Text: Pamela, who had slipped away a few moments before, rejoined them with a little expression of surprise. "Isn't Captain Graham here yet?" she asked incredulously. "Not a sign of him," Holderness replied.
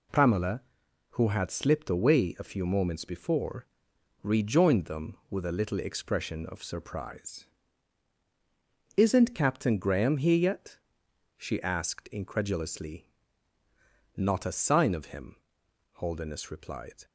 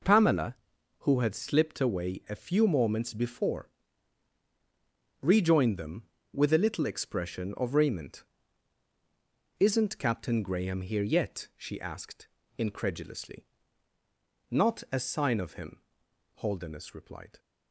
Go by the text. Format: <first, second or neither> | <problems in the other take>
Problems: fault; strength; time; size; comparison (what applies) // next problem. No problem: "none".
first | says "raiment" for "surprise"; at 7.7 s // pauses between "asked" and "incredulously"; slight; at 12.2 s; 0.30 s long